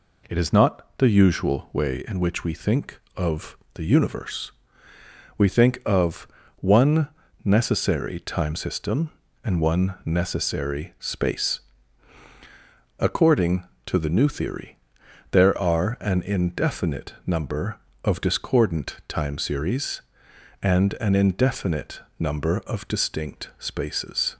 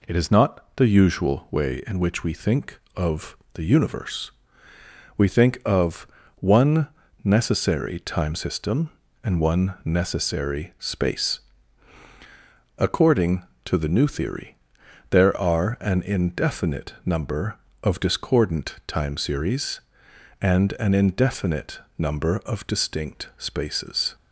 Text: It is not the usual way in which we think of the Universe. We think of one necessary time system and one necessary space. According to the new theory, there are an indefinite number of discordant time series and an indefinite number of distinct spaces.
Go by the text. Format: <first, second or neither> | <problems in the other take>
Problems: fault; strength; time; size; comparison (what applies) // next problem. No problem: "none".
neither | pauses between "of" and "the"; slight; the same in both // pauses between "of" and "one"; slight; the same in both // pauses between "one" and "necessary"; slight; the same in both // pauses between "indefinite" and "number"; slight; the same in both